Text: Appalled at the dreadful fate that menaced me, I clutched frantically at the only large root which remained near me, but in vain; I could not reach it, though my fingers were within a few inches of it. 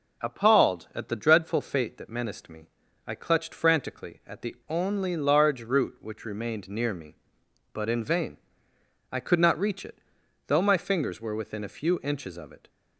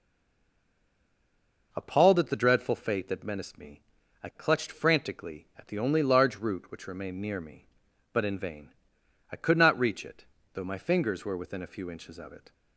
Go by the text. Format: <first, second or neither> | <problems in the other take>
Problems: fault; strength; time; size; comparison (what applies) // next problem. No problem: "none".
first | stays silent before the first word; noticeable; until 1.7 s; 1.7 s long